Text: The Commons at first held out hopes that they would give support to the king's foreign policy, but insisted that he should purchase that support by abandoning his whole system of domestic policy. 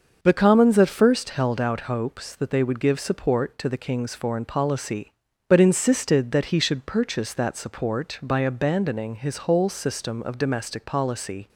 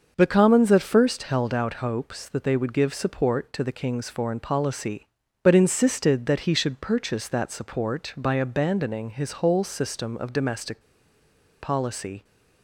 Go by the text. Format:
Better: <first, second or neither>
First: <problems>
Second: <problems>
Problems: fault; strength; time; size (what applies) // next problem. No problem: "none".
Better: first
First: starts louder than the rest; until 1.2 s; 6.5 dB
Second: starts louder than the rest; until 1.1 s; 6.5 dB // pauses between "domestic" and "policy"; noticeable; at 10.8 s; 0.81 s long